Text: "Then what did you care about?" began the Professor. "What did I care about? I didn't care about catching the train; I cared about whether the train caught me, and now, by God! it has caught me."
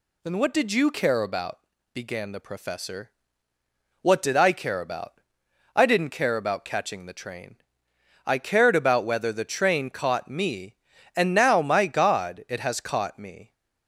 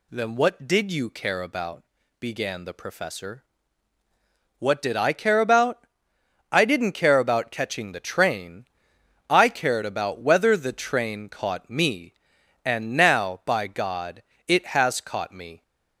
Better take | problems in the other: second | says "my" for "by"; at 11.6 s

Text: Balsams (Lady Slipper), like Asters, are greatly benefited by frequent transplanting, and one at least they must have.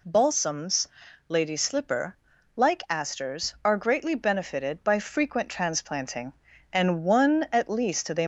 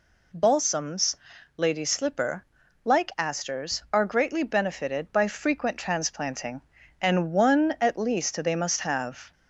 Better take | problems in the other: second | stops before "must have"; at 8.2 s

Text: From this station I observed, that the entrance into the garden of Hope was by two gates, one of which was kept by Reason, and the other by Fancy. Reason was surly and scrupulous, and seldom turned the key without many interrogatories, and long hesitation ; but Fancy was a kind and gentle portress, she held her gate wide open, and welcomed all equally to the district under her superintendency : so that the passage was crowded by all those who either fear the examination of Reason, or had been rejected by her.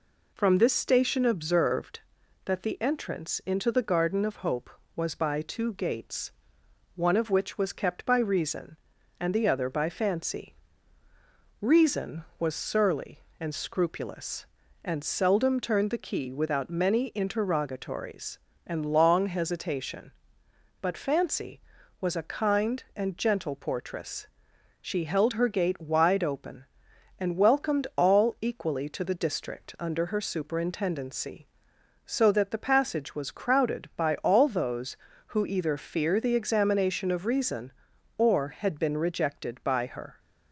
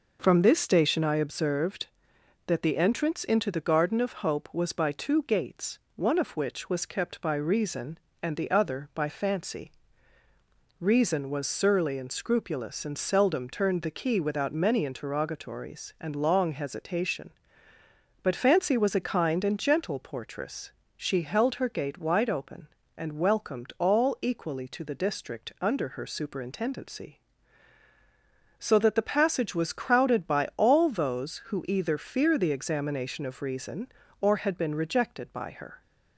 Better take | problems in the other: second | skips "I"; at 1.2 s

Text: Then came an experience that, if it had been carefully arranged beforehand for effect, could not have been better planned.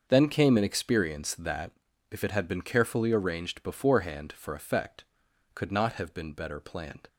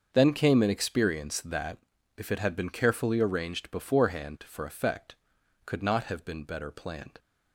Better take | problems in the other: neither | starts louder than the rest; the same in both

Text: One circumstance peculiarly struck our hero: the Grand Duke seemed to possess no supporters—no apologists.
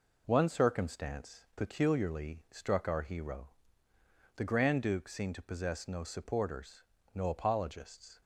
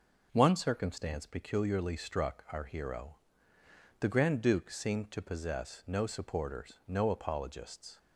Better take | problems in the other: neither | none

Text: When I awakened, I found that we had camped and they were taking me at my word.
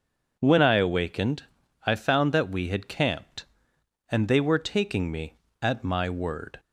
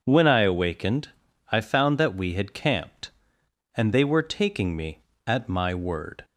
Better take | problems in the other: neither | none

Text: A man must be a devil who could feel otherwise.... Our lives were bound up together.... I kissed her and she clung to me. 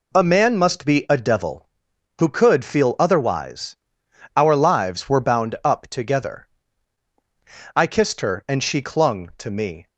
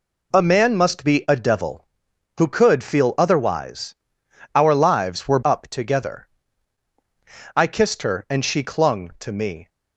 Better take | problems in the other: first | skips "bound"; at 5.4 s

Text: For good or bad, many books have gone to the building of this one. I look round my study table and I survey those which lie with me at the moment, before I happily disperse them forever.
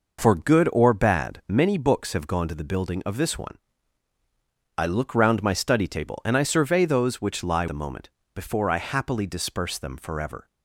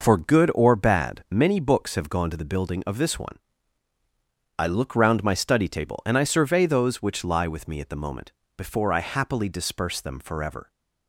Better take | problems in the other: second | skips "with me at"; at 7.6 s

